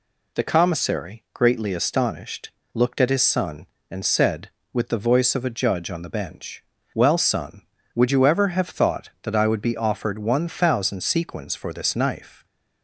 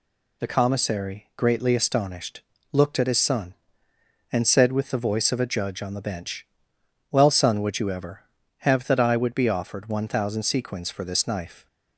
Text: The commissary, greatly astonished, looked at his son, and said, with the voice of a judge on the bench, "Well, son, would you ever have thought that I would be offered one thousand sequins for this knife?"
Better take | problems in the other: first | skips "thought"; at 8.8 s

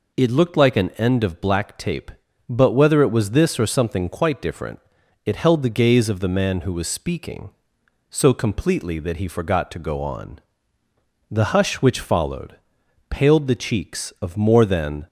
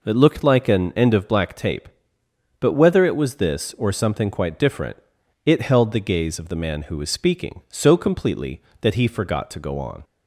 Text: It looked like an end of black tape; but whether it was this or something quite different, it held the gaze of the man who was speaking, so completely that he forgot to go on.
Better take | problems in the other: second | goes on to say "The hush which followed paled the cheeks of more than"; strong; from 11.3 s on; 3.7 s long

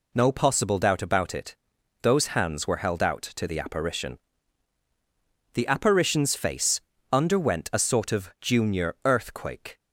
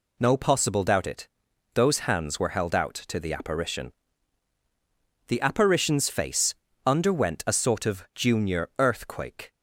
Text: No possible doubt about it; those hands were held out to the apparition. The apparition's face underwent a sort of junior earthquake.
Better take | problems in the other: first | skips "about"; at 1.0 s // pauses between "face" and "underwent"; slight; at 6.5 s; 0.32 s long; slight in the first

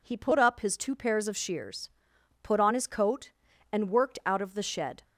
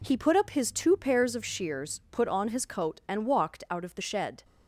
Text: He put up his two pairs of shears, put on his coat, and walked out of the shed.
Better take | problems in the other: second | says "worked" for "walked"; at 3.9 s

